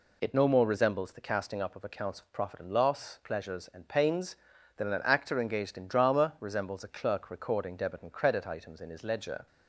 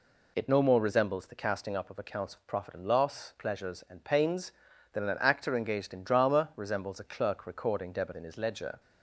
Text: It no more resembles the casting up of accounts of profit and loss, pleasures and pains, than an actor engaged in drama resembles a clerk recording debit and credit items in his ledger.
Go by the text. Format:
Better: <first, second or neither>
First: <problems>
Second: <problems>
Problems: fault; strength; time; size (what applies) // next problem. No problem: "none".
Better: first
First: none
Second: skips "and credit items"; at 8.1 s